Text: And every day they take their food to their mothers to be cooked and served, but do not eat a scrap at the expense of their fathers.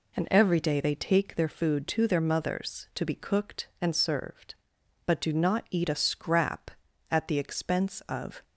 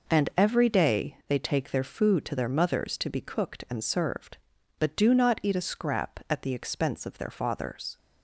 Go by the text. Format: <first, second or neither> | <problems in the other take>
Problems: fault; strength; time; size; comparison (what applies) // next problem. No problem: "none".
second | stops before "their fathers"; at 8.4 s